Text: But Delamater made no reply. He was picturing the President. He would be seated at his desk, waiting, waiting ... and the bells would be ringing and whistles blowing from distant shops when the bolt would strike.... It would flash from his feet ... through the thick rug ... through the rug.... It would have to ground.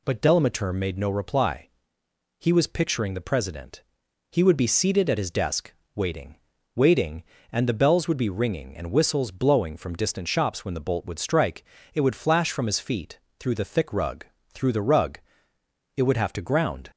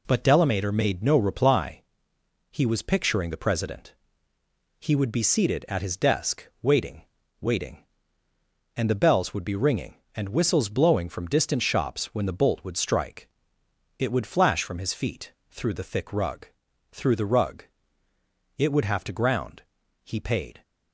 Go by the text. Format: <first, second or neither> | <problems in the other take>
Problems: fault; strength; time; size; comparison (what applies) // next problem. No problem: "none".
first | goes on to say "He paid"; from 20.0 s on; 0.58 s long